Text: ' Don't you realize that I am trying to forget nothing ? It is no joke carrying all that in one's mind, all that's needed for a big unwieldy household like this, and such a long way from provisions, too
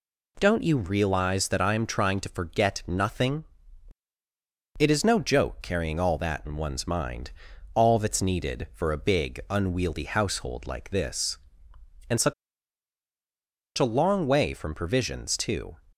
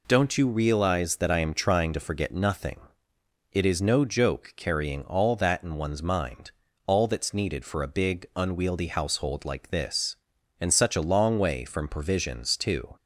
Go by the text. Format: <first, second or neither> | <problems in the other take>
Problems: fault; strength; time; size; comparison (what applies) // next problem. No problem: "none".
second | pauses between "such" and "a"; strong; at 12.3 s; 1.4 s long